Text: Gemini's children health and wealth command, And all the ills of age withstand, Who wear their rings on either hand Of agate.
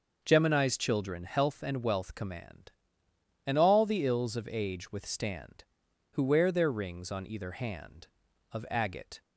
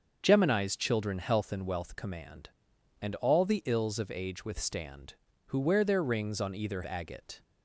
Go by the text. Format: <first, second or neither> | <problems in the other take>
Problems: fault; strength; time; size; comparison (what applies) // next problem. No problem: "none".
first | starts louder than the rest; until 1.2 s; 7 dB; noticeable in the first // skips "hand Of"; at 6.8 s